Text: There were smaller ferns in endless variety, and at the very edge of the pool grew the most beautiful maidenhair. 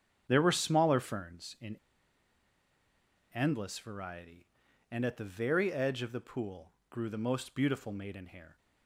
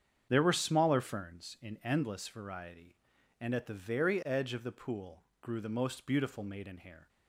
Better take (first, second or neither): second